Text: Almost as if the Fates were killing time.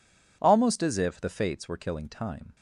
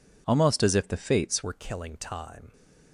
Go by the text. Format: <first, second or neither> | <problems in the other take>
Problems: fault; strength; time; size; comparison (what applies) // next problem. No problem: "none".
first | changes voice at "were"; from 1.4 s on; 1.1 s long